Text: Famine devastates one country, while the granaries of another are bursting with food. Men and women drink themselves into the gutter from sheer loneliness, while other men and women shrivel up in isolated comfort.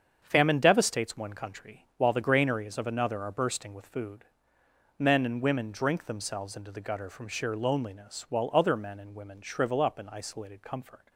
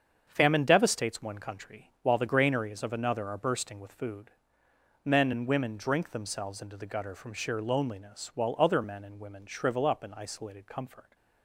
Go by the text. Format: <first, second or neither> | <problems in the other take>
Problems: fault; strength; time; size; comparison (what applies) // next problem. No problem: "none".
neither | starts louder than the rest; strong; the same in both